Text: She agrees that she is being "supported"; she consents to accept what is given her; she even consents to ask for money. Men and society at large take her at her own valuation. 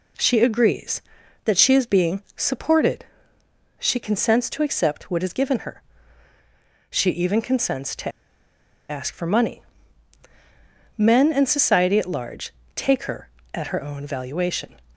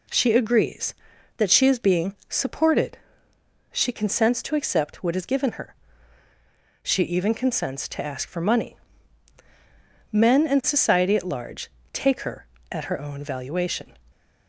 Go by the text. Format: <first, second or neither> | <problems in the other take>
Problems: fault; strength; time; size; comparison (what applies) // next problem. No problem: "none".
second | pauses between "being" and "supported"; slight; at 2.2 s; 0.16 s long; slight in the second // pauses between "to" and "ask"; noticeable; at 8.0 s; 0.79 s long // pauses between "large" and "take"; slight; at 12.5 s; 0.24 s long; slight in the second